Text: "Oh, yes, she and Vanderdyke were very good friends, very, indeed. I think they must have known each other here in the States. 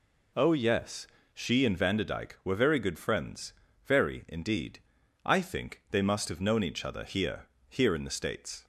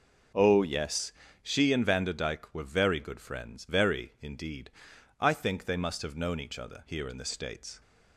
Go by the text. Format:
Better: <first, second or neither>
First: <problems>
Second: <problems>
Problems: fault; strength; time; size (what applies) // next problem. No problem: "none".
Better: second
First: says "here" twice; at 7.6 s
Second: none